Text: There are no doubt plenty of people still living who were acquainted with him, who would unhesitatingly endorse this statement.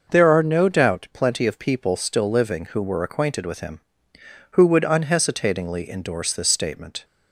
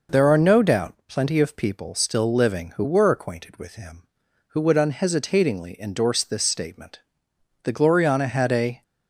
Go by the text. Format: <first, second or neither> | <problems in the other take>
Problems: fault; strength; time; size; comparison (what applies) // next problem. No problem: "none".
first | goes on to say "The Gloriana had a"; noticeable; from 7.6 s on; 1.2 s long